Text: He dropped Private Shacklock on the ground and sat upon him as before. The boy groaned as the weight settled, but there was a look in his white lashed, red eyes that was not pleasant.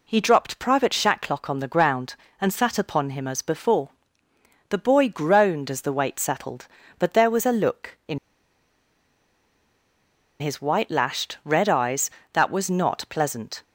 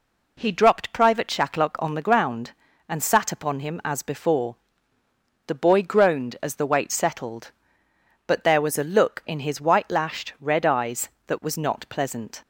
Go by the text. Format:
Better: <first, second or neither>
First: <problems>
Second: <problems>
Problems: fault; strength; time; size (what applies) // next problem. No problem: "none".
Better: second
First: pauses between "in" and "his"; strong; at 8.1 s; 2.2 s long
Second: none